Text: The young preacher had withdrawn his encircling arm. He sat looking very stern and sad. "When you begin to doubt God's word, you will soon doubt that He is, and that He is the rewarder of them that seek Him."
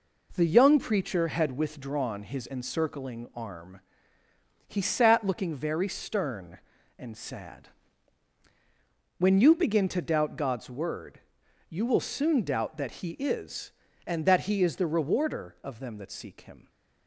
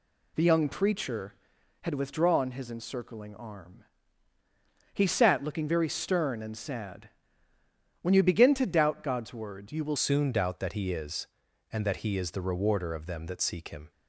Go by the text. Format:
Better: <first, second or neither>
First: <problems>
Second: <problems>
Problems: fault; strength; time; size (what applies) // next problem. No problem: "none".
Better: first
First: none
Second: changes voice at "soon"; from 9.9 s on; 4.0 s long